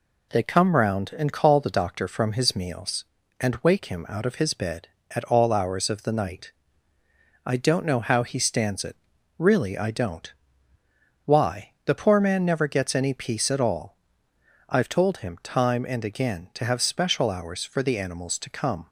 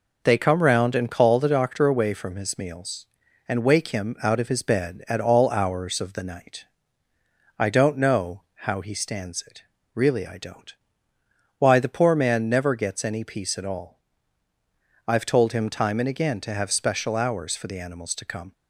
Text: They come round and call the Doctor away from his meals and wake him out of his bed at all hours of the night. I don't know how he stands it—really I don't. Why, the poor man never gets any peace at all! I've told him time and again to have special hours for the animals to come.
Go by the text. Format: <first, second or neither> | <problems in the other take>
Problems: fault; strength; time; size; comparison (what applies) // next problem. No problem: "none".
second | skips "away"; at 2.0 s